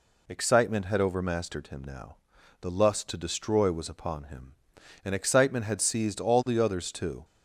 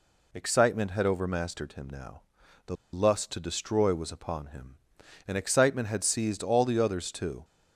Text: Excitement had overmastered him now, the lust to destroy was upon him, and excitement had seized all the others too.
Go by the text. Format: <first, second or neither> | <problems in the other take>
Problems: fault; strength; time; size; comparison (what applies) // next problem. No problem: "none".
first | pauses between "the" and "lust"; slight; at 2.7 s; 0.18 s long